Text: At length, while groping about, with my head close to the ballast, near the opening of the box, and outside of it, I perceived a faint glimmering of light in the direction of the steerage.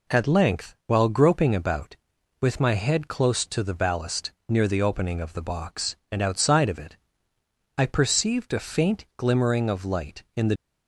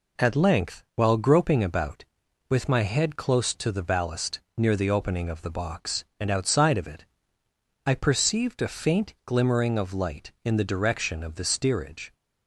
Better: second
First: stops before "direction of the steerage"; at 10.5 s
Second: none

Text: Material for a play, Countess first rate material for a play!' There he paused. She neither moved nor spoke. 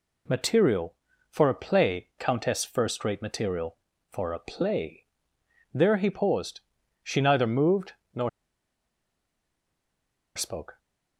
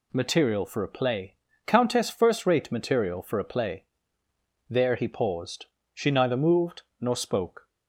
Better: second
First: pauses between "moved" and "nor"; slight; at 7.9 s; 0.20 s long // pauses between "nor" and "spoke"; strong; at 8.2 s; 2.0 s long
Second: pauses between "moved" and "nor"; slight; at 6.8 s; 0.18 s long

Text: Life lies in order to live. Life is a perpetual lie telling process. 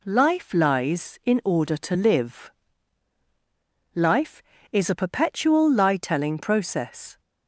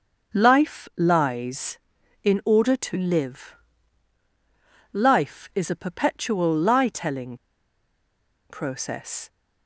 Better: first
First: none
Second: starts louder than the rest; until 1.4 s; 6.5 dB // pauses between "telling" and "process"; at 7.3 s; 1.1 s long

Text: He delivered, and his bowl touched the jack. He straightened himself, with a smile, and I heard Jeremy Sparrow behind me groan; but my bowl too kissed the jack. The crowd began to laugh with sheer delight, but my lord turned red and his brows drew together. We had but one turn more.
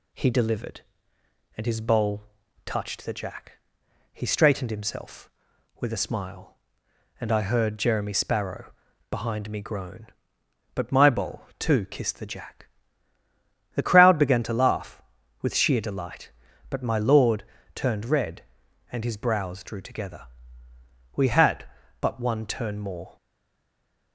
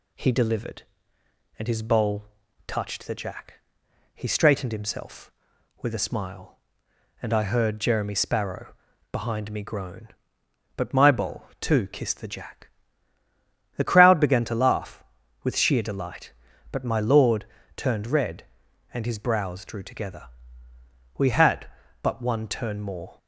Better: second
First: pauses between "bowl" and "touched"; at 2.2 s; 0.42 s long // pauses between "Sparrow" and "behind"; at 8.7 s; 0.38 s long // pauses between "lord" and "turned"; slight; at 17.4 s; 0.30 s long // stays silent after the last word; from 23.1 s on; 1.0 s long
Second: pauses between "bowl" and "touched"; at 2.2 s; 0.42 s long // pauses between "Sparrow" and "behind"; at 8.7 s; 0.38 s long // pauses between "lord" and "turned"; slight; at 17.4 s; 0.30 s long

